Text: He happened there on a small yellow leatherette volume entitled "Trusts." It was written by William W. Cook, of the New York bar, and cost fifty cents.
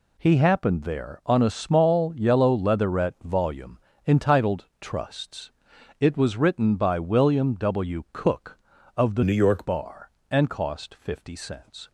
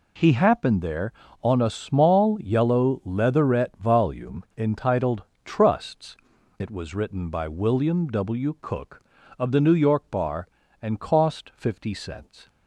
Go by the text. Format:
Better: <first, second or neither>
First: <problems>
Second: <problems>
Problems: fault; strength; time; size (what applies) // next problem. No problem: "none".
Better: second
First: pauses between "volume" and "entitled"; slight; at 3.7 s; 0.30 s long // pauses between "entitled" and "Trusts"; slight; at 4.6 s; 0.16 s long // changes voice from "New" to "York"; from 9.2 to 9.6 s; 0.4 s long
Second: pauses between "entitled" and "Trusts"; slight; at 5.2 s; 0.22 s long